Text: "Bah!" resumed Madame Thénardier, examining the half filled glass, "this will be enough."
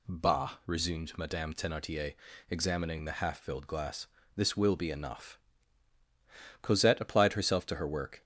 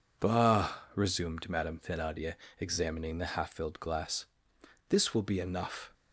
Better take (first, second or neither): second